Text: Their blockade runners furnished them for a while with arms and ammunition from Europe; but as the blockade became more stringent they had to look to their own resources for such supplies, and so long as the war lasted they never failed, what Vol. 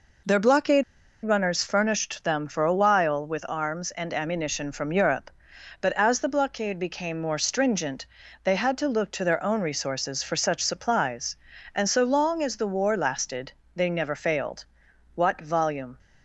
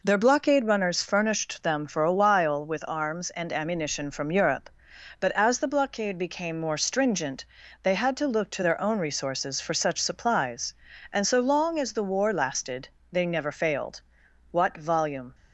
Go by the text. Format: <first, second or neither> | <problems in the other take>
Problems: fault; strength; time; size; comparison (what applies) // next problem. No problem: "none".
second | pauses between "blockade" and "runners"; at 0.8 s; 0.40 s long // pauses between "stringent" and "they"; at 8.0 s; 0.38 s long; also in the second // pauses between "lasted" and "they"; slight; at 13.5 s; 0.24 s long; slight in the second